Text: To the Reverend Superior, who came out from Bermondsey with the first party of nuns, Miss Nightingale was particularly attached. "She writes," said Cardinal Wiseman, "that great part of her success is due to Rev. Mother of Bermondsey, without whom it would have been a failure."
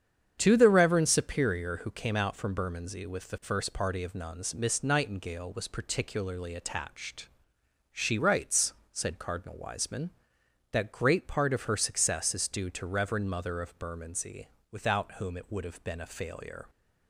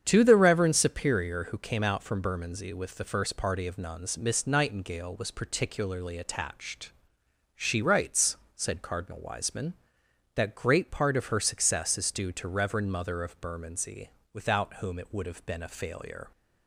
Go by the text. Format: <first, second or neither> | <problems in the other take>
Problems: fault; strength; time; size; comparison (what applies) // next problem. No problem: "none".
neither | starts louder than the rest; strong; the same in both